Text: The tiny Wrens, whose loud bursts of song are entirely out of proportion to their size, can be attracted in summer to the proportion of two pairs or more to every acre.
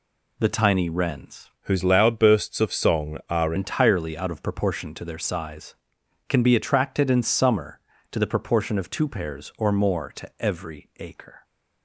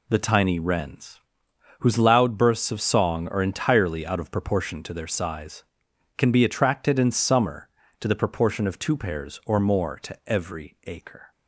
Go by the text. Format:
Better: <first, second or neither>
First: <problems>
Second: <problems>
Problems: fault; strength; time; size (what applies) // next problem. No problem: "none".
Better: second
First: changes voice from "whose" to "are"; from 1.6 to 3.5 s; 1.9 s long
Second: none